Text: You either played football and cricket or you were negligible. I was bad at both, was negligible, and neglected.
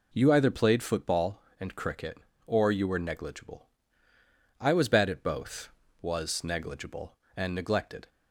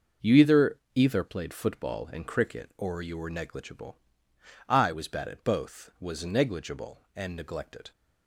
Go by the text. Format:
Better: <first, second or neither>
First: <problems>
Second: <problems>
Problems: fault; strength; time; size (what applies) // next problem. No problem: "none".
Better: first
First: none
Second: says "either" twice; at 0.9 s